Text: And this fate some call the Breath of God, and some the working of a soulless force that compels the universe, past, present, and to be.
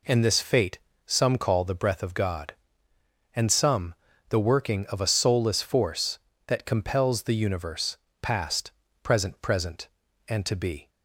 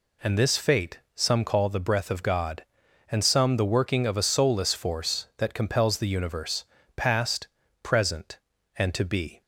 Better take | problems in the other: second | pauses between "fate" and "some"; slight; at 0.7 s; 0.26 s long; slight in the second // pauses between "some" and "the"; slight; at 3.9 s; 0.36 s long // says "present" twice; at 9.4 s

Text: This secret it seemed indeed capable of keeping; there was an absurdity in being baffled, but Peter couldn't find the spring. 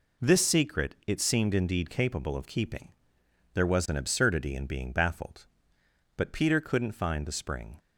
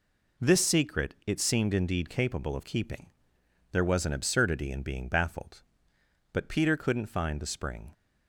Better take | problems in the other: neither | none

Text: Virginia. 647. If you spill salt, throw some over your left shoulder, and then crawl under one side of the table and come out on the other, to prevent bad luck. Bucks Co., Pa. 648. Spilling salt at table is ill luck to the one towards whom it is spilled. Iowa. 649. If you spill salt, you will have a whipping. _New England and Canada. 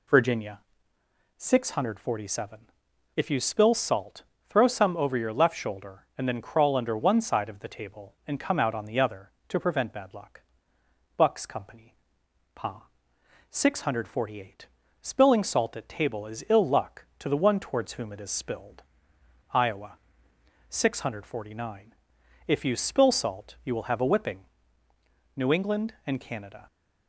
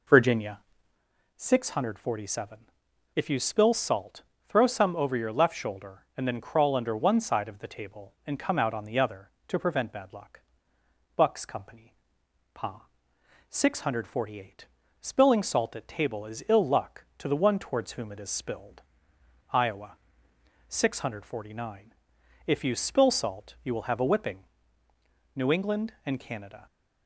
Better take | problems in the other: first | starts louder than the rest; noticeable; until 1.0 s; 4.5 dB

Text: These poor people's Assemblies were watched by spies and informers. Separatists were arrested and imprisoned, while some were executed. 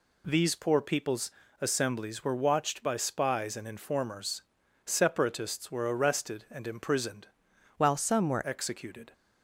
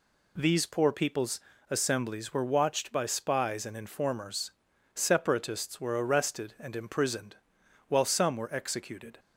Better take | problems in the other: second | pauses between "people's" and "Assemblies"; slight; at 1.2 s; 0.32 s long; slight in the second // changes voice from "while" to "were"; from 7.7 to 8.4 s; 0.7 s long

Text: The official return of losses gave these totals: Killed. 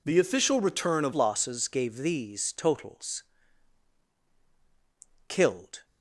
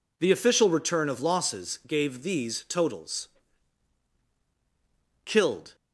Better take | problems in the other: second | changes voice at "losses"; from 1.1 s on; 4.7 s long

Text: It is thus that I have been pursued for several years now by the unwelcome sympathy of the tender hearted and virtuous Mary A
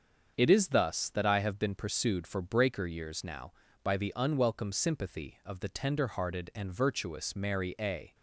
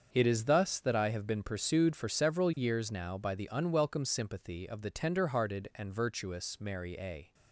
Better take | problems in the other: second | starts louder than the rest; until 1.3 s; 7 dB; also in the second // says "breaker" for "several"; at 2.4 s

